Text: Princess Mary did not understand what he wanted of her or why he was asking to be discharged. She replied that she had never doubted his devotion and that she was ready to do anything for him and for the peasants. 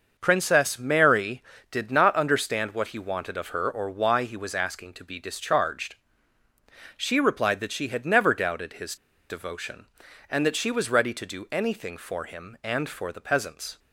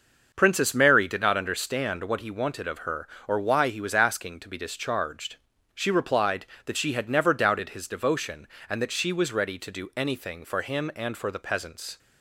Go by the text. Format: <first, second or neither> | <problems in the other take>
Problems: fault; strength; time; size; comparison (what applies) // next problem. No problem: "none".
second | starts louder than the rest; until 1.1 s; 6 dB; noticeable in the second // pauses between "his" and "devotion"; slight; at 8.9 s; 0.34 s long